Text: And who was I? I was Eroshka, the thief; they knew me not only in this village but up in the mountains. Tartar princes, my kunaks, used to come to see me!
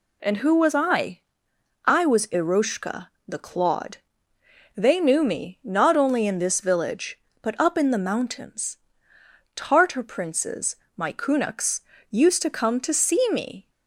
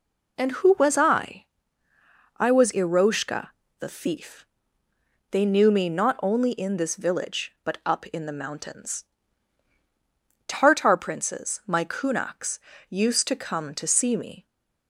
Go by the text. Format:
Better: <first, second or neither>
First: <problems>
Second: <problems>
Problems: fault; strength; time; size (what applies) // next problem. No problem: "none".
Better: second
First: says "clawed" for "thief"; at 3.3 s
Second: none